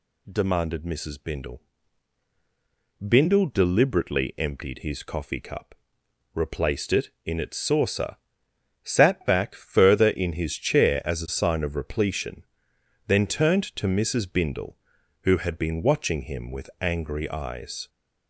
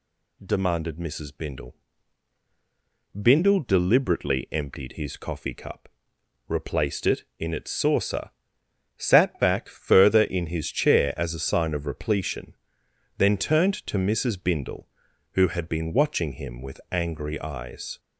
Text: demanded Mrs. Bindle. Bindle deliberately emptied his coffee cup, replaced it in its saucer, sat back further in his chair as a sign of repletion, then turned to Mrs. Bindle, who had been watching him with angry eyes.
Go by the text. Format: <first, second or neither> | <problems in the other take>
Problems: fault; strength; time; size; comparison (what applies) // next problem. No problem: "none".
neither | none